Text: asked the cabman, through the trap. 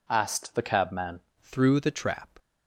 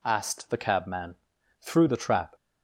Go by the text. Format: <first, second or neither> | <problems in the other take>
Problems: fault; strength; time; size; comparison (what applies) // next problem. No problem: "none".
second | changes voice at "through"; from 1.4 s on; 0.8 s long